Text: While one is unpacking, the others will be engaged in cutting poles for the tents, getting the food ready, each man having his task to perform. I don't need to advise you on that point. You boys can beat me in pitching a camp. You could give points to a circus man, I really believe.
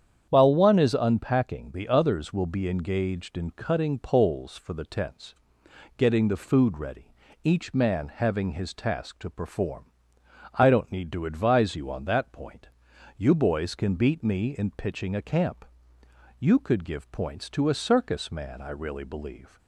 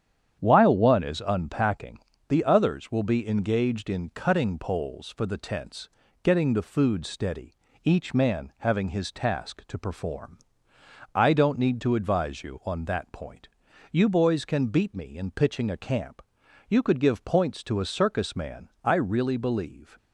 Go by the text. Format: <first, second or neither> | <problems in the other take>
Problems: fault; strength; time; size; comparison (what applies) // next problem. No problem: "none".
first | starts louder than the rest; strong; until 1.4 s; 9 dB; strong in the first // says "steady" for "ready"; at 7.0 s